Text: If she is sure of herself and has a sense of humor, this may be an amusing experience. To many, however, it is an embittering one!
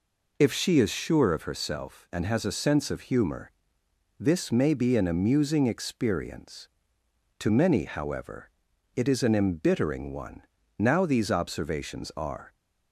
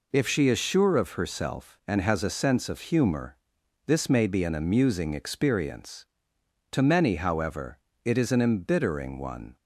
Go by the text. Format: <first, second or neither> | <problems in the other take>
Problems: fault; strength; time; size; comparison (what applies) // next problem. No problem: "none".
second | goes on to say "Now these observations are"; strong; from 10.7 s on; 1.7 s long